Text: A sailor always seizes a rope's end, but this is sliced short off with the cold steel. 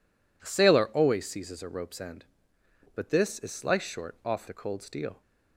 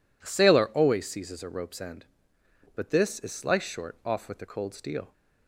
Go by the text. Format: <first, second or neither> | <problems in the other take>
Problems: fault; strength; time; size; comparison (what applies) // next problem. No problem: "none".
second | skips "with"; at 4.4 s